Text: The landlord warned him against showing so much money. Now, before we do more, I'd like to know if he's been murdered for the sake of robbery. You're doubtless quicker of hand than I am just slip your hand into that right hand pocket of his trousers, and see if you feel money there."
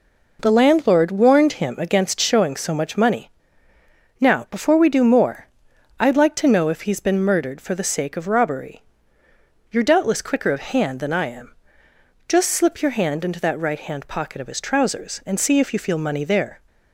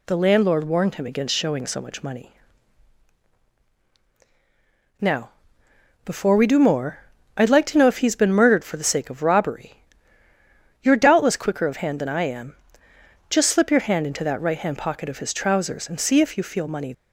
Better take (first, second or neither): first